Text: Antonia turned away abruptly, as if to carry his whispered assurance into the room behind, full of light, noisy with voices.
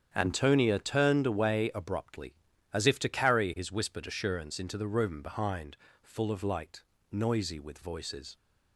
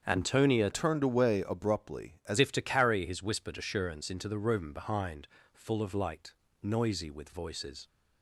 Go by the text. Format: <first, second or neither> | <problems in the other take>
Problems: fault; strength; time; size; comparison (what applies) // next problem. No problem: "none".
first | starts louder than the rest; strong; until 1.0 s; 7.5 dB; strong in the first // changes voice from "turned" to "as"; from 0.7 to 2.3 s; 1.6 s long